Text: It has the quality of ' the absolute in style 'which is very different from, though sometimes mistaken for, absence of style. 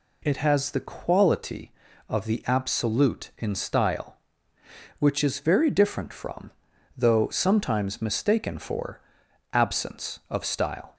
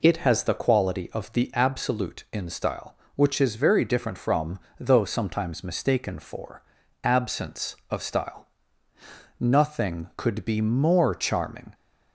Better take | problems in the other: first | goes on to say "Nothing could be more charming"; strong; from 9.3 s on; 2.3 s long

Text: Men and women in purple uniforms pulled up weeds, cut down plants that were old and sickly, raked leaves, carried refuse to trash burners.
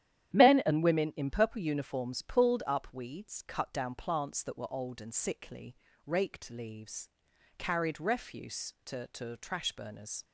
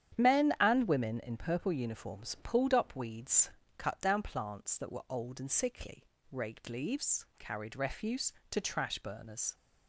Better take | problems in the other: second | starts louder than the rest; strong; until 1.3 s; 11 dB; strong in the second // says "to" twice; at 9.0 s

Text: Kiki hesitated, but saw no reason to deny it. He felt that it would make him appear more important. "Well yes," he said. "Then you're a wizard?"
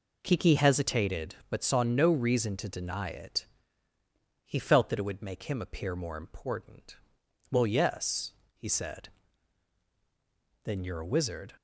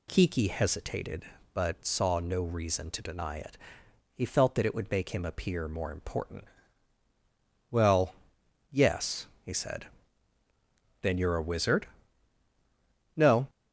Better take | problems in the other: first | pauses between "Well" and "yes"; noticeable; at 8.1 s; 0.56 s long // goes on to say "No"; slight; from 13.1 s on; 0.34 s long

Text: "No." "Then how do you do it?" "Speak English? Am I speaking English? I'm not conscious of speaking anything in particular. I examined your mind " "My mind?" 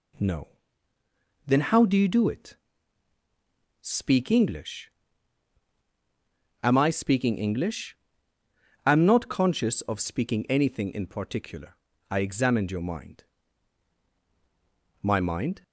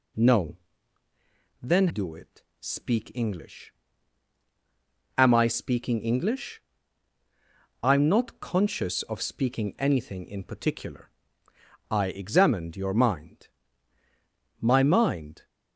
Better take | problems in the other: first | skips "how do you"; at 1.8 s

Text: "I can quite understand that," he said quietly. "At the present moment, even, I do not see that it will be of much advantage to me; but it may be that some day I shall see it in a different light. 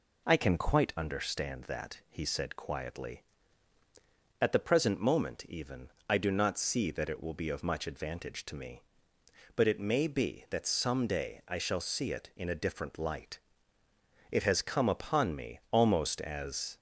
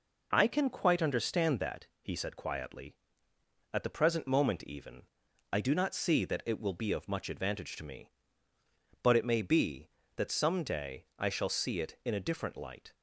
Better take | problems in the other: second | goes on to say "It has come upon me almost as"; strong; from 14.3 s on; 2.4 s long

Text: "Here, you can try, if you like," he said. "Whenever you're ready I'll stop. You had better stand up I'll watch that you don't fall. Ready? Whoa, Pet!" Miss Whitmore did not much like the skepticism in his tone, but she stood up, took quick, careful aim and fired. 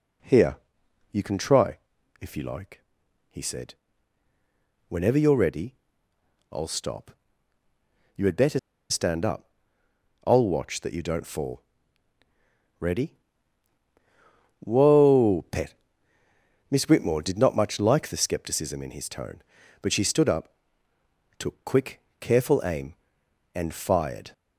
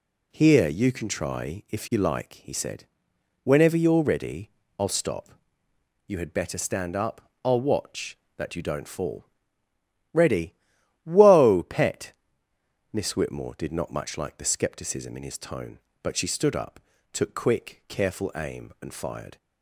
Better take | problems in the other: second | pauses between "ready" and "I'll"; noticeable; at 5.7 s; 0.78 s long; slight in the second // pauses between "better" and "stand"; slight; at 8.5 s; 0.31 s long // pauses between "up" and "I'll"; noticeable; at 9.4 s; 0.76 s long; slight in the second

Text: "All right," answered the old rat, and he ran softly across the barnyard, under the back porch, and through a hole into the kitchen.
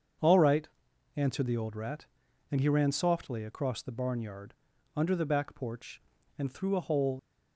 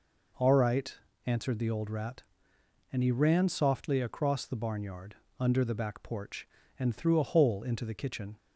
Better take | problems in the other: second | starts louder than the rest; until 1.6 s; 7 dB // stops before "into the kitchen"; at 7.1 s

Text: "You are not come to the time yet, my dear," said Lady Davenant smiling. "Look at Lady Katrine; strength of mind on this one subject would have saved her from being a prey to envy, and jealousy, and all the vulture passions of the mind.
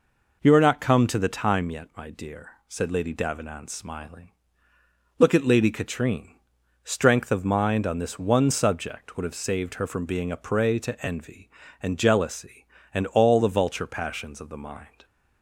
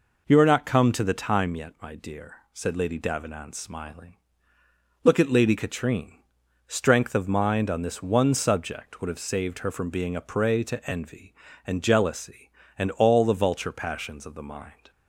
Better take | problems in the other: neither | none

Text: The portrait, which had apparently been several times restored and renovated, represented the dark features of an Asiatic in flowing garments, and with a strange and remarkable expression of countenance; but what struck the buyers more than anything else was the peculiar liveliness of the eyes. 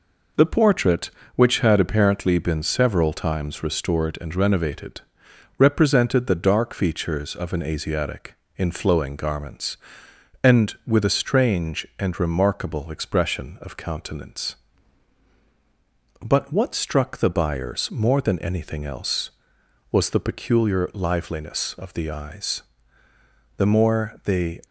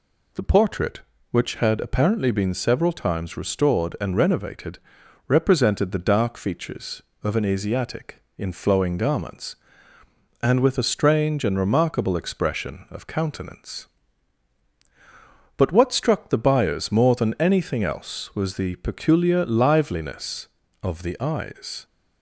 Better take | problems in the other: second | goes on to say "The more they"; noticeable; from 23.5 s on; 1.0 s long

